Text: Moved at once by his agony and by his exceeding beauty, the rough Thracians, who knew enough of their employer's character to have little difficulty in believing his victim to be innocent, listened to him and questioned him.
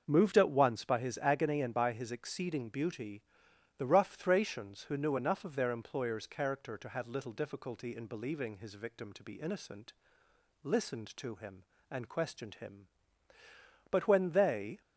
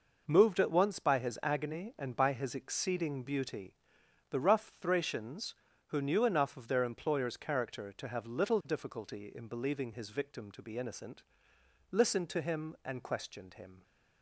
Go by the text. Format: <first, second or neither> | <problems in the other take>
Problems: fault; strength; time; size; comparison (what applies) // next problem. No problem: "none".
second | starts louder than the rest; until 1.0 s; 6.5 dB // goes on to say "But when they"; noticeable; from 13.9 s on; 0.90 s long